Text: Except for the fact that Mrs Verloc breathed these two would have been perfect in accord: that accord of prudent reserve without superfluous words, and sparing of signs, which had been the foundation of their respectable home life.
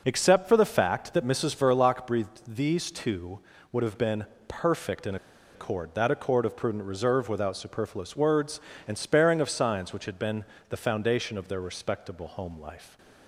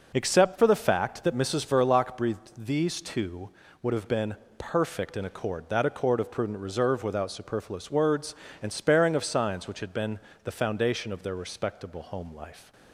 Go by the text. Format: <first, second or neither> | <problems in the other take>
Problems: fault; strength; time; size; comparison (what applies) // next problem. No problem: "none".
second | pauses between "been" and "perfect"; slight; at 4.2 s; 0.20 s long; slight in the second // pauses between "in" and "accord"; at 5.1 s; 0.38 s long // pauses between "been" and "the"; slight; at 10.4 s; 0.26 s long; slight in the second // stays silent after the last word; slight; from 12.7 s on; 0.5 s long